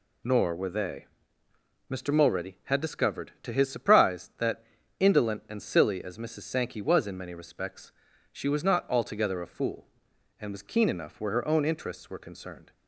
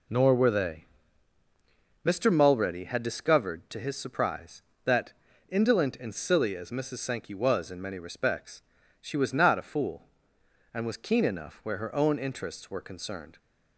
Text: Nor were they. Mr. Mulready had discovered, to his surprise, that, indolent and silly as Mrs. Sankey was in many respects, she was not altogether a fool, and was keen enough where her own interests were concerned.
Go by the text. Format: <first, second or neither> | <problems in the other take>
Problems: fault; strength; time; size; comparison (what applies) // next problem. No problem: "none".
first | skips "altogether"; at 9.5 s